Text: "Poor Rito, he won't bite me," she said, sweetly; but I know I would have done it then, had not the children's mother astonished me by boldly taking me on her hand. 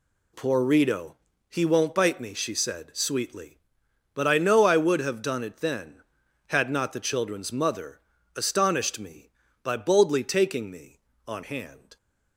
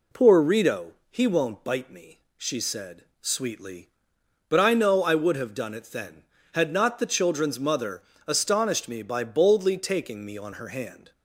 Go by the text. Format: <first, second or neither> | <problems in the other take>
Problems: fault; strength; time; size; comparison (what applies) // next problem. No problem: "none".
second | pauses between "mother" and "astonished"; slight; at 7.9 s; 0.36 s long; slight in the second // skips "her"; at 11.4 s